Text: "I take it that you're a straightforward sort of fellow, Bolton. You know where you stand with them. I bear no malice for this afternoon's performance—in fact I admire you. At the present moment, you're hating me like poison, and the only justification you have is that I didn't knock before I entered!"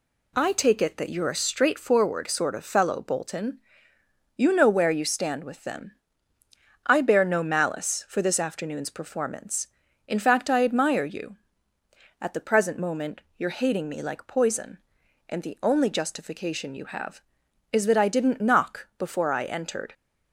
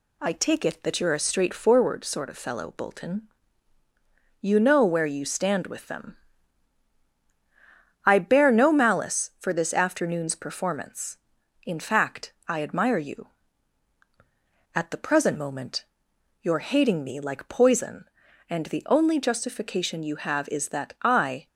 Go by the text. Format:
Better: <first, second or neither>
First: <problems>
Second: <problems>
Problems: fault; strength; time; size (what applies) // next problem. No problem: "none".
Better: first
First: none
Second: stops before "didn't knock before I entered"; at 21.4 s